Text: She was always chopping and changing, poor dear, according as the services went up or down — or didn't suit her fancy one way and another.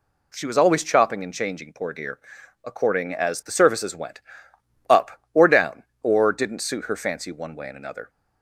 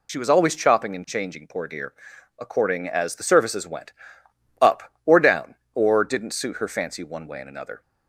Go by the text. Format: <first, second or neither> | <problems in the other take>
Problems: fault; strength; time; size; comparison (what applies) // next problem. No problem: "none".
first | loses the start of "She"; at 0.0 s; 40 ms // pauses between "went" and "up"; noticeable; at 3.9 s; 0.68 s long; noticeable in the first